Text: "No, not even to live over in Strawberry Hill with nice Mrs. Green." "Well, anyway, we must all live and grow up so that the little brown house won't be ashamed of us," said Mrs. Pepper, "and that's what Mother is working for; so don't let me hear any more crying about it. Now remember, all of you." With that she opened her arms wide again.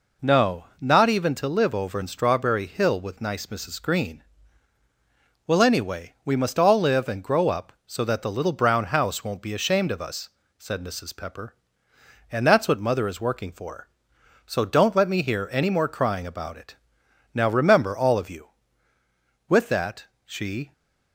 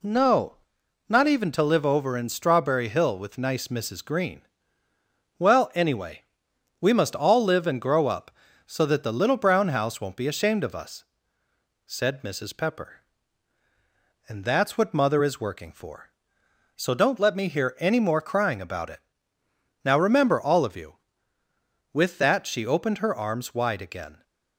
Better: second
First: pauses between "that" and "she"; slight; at 20.0 s; 0.20 s long // stops before "opened her arms wide again"; at 20.7 s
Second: none

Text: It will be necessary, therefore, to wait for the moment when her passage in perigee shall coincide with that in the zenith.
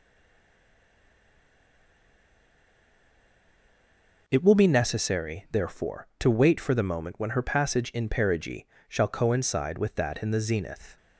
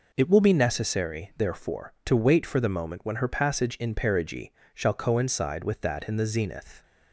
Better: second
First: stays silent before the first word; strong; until 4.2 s; 4.2 s long // pauses between "perigee" and "shall"; slight; at 8.6 s; 0.24 s long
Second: pauses between "perigee" and "shall"; slight; at 4.5 s; 0.24 s long

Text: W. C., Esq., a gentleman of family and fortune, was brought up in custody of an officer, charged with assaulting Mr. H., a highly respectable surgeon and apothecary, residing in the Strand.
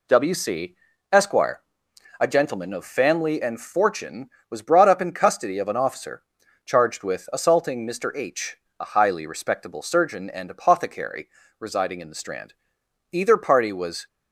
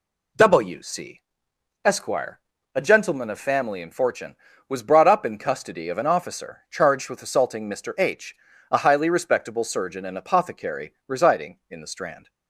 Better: second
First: goes on to say "Either party was"; noticeable; from 13.1 s on; 0.94 s long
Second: none

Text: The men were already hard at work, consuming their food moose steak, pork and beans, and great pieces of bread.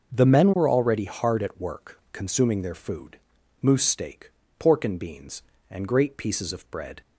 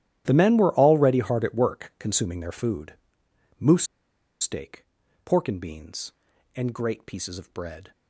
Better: first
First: starts louder than the rest; noticeable; until 1.1 s; 6 dB // pauses between "food" and "moose"; noticeable; at 3.1 s; 0.46 s long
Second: starts louder than the rest; strong; until 1.2 s; 12 dB // pauses between "food" and "moose"; noticeable; at 2.9 s; 0.66 s long // pauses between "moose" and "steak"; noticeable; at 3.8 s; 0.56 s long

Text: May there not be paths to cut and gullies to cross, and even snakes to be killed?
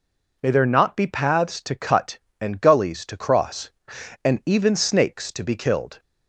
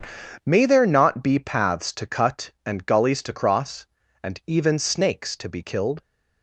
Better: neither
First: none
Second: none

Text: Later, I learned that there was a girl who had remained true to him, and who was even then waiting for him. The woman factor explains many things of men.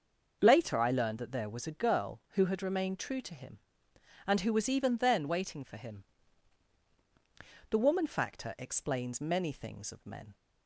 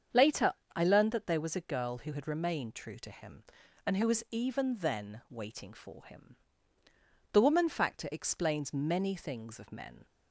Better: neither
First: starts louder than the rest; until 1.4 s; 6 dB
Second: starts louder than the rest; strong; until 1.3 s; 7.5 dB

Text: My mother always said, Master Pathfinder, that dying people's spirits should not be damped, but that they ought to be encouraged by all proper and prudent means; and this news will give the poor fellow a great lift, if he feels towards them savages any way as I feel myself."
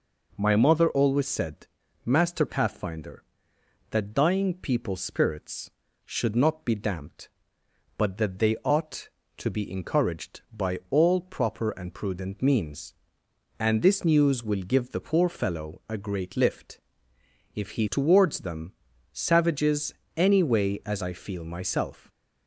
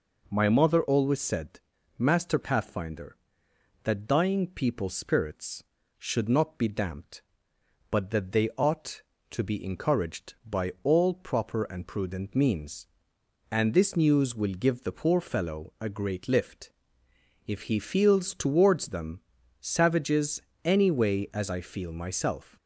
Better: second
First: skips "feels"; at 17.8 s // pauses between "them" and "savages"; at 18.7 s; 0.40 s long // pauses between "savages" and "any"; slight; at 19.9 s; 0.22 s long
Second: pauses between "them" and "savages"; at 19.1 s; 0.40 s long // pauses between "savages" and "any"; slight; at 20.4 s; 0.22 s long

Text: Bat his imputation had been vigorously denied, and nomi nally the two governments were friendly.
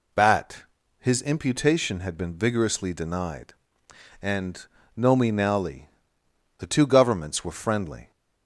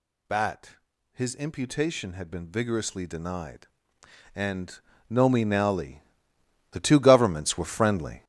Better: first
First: pauses between "Bat" and "his"; slight; at 0.6 s; 0.36 s long // pauses between "and" and "nomi"; slight; at 4.6 s; 0.28 s long // pauses between "nally" and "the"; noticeable; at 5.8 s; 0.70 s long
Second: gets louder; strong; throughout; 8.5 dB // pauses between "Bat" and "his"; slight; at 0.7 s; 0.36 s long // pauses between "and" and "nomi"; slight; at 4.7 s; 0.28 s long // pauses between "nally" and "the"; noticeable; at 6.0 s; 0.70 s long

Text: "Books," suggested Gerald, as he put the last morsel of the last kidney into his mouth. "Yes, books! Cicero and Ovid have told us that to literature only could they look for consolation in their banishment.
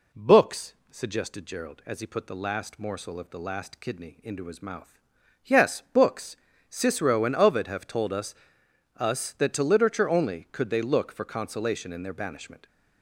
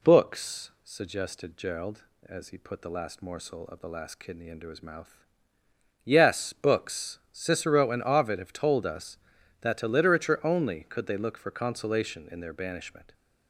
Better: second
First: says "us" twice; at 8.9 s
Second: none

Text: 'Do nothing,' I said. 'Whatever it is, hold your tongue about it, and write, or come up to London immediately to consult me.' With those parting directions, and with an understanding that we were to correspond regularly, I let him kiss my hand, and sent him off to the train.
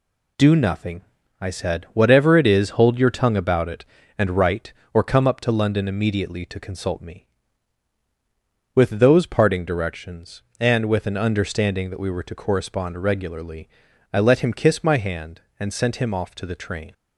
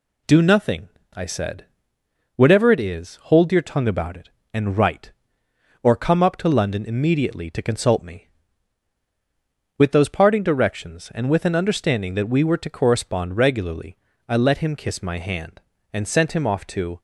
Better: first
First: none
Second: stops before "the train"; at 16.9 s

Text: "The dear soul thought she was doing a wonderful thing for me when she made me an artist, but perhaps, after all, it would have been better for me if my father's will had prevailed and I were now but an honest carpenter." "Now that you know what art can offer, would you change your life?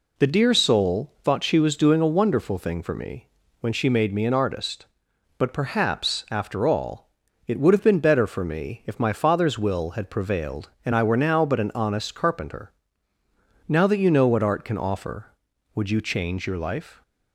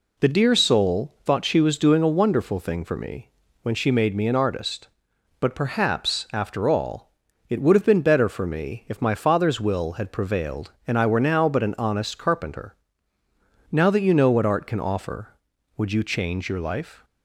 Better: neither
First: pauses between "me" and "when"; slight; at 3.2 s; 0.32 s long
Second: pauses between "me" and "when"; slight; at 3.2 s; 0.32 s long

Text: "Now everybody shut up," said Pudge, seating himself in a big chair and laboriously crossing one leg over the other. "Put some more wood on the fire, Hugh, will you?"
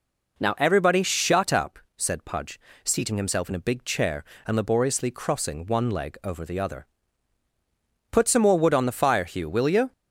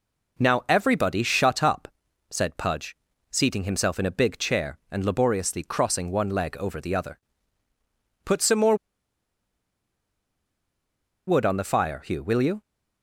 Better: first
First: none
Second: pauses between "more" and "wood"; strong; at 8.7 s; 2.5 s long

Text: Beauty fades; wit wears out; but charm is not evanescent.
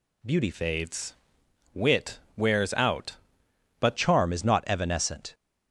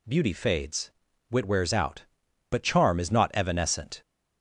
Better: second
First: changes voice from "fades" to "but"; from 0.5 to 3.9 s; 3.4 s long // pauses between "wit" and "wears"; slight; at 2.1 s; 0.16 s long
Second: none

